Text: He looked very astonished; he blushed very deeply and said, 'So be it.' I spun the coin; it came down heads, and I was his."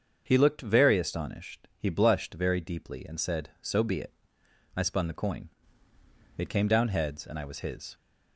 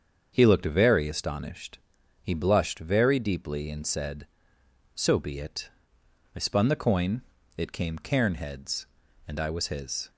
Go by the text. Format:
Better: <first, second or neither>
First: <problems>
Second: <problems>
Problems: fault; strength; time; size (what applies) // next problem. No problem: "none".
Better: first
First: starts louder than the rest; until 1.2 s; 7 dB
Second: starts louder than the rest; until 1.3 s; 7 dB // says "cairn" for "down"; at 7.9 s